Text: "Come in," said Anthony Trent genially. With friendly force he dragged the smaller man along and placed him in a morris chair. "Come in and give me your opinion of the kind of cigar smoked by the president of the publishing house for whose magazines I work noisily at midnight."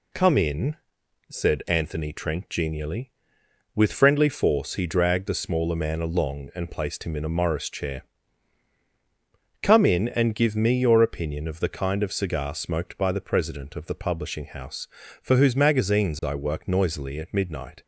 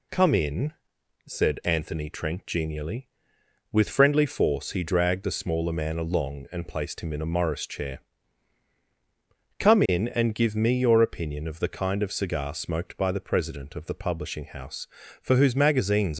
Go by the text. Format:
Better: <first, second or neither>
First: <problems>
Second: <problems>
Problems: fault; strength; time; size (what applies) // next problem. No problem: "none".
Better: first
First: none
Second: stops before "I work noisily at midnight"; at 16.1 s